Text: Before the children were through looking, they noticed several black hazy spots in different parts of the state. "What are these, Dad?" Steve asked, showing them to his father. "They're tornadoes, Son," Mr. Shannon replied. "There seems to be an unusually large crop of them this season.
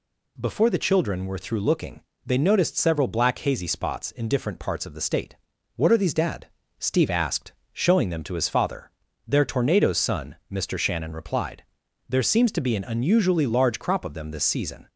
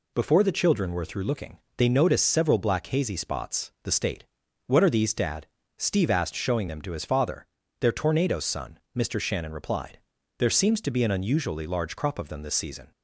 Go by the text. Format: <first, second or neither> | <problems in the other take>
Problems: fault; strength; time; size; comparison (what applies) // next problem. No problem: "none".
first | skips "in different parts of"; at 3.7 s